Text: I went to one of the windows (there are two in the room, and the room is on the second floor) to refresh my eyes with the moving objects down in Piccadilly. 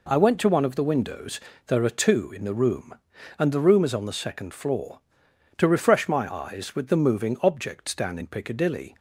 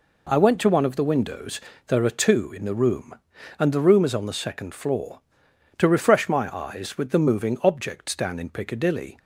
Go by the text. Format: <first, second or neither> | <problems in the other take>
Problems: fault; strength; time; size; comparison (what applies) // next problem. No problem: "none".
neither | none